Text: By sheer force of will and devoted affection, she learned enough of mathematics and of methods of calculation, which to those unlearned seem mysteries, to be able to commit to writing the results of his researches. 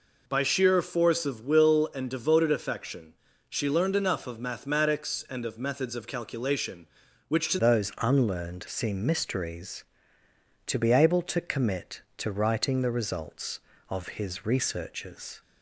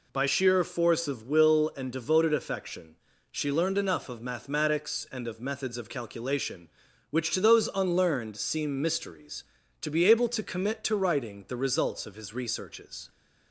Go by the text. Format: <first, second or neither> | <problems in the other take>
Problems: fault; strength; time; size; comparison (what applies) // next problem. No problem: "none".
second | changes voice at "those"; from 7.5 s on; 7.9 s long